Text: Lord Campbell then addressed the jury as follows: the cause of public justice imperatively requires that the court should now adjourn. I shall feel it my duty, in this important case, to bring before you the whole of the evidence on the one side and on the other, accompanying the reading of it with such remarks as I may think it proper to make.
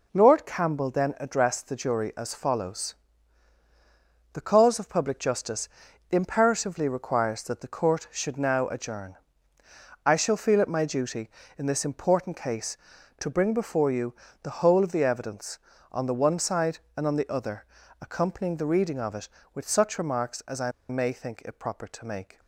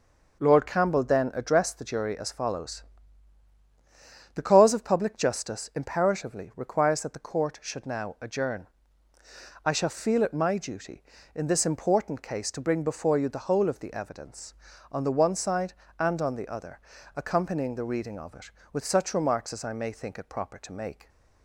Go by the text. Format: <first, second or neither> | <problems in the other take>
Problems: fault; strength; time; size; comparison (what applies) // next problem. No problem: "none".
second | pauses between "justice" and "imperatively"; at 5.6 s; 0.42 s long // pauses between "you" and "the"; slight; at 14.1 s; 0.26 s long // pauses between "I" and "may"; slight; at 20.7 s; 0.17 s long